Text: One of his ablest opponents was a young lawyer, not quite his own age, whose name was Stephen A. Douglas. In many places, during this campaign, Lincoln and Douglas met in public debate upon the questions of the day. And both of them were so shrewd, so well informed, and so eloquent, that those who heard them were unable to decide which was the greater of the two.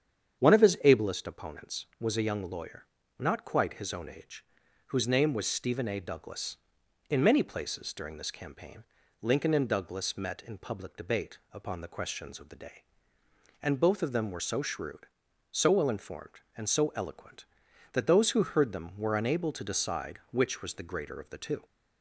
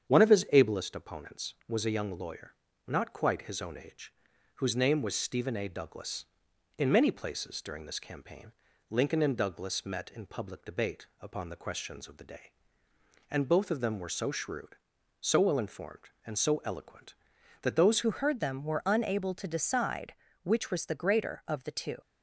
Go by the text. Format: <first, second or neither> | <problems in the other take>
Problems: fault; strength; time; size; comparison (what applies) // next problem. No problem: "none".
first | starts louder than the rest; strong; until 1.1 s; 8 dB; strong in the first // changes voice at "who"; from 18.0 s on; 3.9 s long